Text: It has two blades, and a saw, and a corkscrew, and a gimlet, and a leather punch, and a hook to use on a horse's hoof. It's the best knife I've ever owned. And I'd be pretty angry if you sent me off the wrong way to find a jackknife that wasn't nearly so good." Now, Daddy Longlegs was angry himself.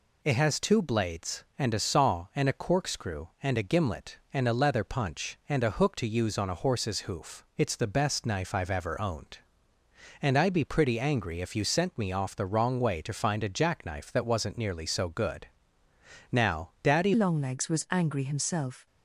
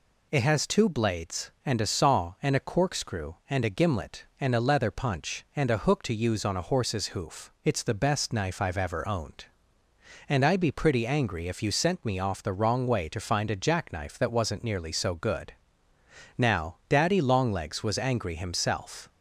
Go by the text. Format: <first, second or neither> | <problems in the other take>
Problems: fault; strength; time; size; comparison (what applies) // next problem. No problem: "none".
second | changes voice at "Longlegs"; from 17.1 s on; 1.7 s long